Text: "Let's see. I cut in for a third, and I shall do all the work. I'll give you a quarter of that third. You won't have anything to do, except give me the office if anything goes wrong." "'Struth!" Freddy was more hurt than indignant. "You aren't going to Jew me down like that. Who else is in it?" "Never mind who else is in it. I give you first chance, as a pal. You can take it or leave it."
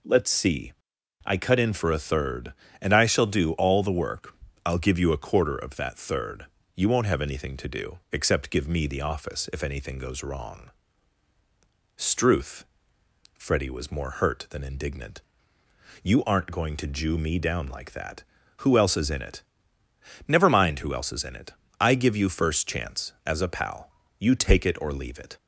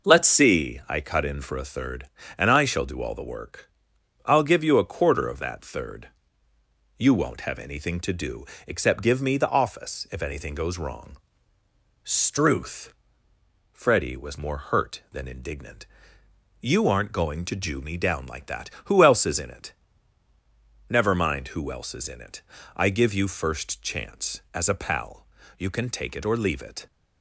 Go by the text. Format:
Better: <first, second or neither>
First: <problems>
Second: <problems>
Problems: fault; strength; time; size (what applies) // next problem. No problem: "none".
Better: second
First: skips "can"; at 24.3 s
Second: none